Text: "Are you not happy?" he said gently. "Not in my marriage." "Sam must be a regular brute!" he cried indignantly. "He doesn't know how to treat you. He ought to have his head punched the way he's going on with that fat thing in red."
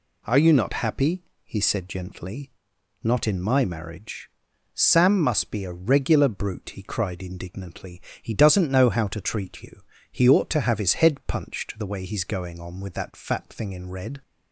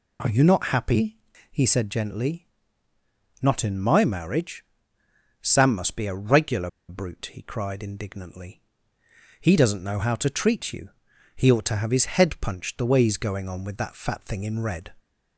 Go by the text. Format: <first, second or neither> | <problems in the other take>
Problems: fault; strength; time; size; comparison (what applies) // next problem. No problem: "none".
first | pauses between "regular" and "brute"; slight; at 6.6 s; 0.19 s long